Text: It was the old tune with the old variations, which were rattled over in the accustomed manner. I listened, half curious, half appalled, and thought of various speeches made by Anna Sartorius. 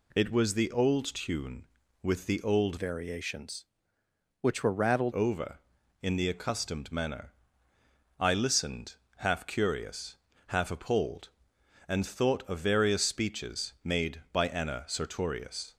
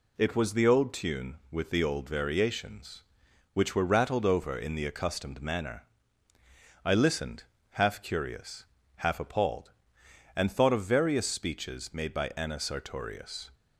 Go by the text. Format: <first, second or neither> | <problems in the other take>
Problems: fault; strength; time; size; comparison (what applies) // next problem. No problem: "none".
second | changes voice from "variations" to "rattled"; from 2.7 to 5.1 s; 2.4 s long